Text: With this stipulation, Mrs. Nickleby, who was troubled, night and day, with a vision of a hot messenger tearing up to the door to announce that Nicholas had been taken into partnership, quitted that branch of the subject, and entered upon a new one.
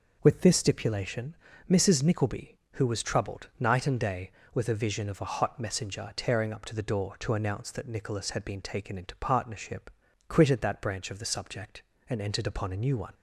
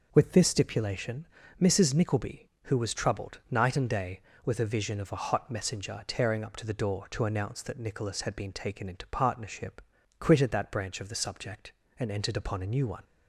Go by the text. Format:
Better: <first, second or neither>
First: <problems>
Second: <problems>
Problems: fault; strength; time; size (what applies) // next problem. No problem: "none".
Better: neither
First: none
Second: none